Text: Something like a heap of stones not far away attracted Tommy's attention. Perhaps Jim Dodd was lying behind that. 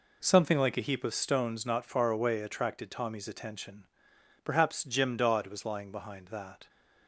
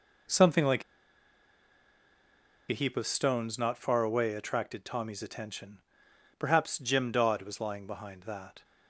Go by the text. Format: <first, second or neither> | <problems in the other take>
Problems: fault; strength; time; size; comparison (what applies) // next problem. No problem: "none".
first | pauses between "like" and "a"; strong; at 0.8 s; 1.8 s long